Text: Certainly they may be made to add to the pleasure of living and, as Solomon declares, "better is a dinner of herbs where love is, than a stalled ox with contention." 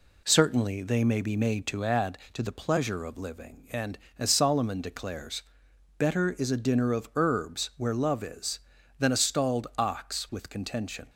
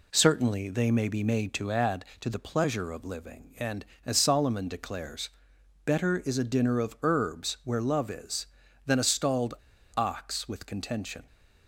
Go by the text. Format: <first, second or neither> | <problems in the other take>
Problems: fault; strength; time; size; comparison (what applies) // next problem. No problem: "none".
first | pauses between "stalled" and "ox"; at 9.5 s; 0.41 s long